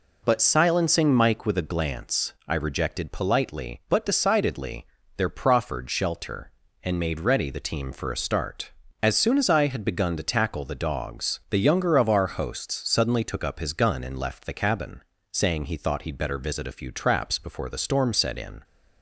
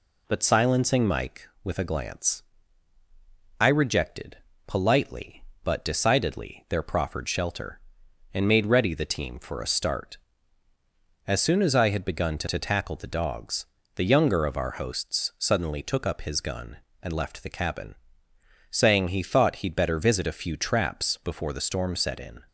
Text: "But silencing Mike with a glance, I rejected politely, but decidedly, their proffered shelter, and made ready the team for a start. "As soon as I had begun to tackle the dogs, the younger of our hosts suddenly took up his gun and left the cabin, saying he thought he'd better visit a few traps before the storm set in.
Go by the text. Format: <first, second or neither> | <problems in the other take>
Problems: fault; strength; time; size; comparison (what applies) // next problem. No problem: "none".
first | pauses between "rejected" and "politely"; slight; at 4.3 s; 0.28 s long // says "to" twice; at 12.4 s